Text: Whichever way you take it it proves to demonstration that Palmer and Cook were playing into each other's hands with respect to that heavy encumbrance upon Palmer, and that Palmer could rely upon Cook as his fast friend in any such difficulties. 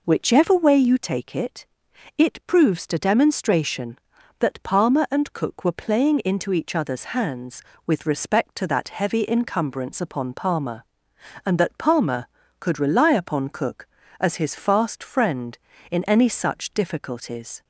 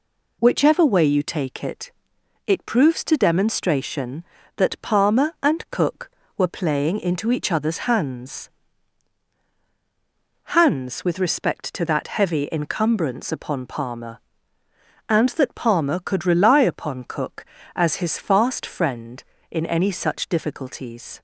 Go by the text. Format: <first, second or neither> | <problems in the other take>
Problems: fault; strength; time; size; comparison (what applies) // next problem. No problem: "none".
first | pauses between "it" and "it"; noticeable; at 1.9 s; 0.54 s long; noticeable in the first // says "hands" twice; at 10.4 s